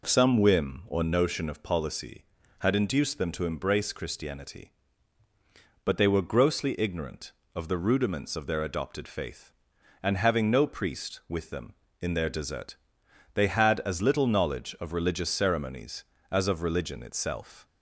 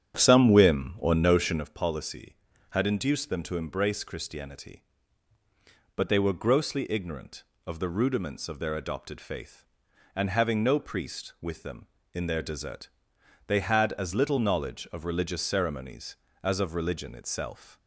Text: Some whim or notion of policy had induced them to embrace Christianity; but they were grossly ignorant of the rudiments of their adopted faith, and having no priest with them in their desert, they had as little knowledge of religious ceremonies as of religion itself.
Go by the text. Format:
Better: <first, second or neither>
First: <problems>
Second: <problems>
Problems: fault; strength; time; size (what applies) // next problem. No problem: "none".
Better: first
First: none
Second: starts louder than the rest; strong; until 1.7 s; 9 dB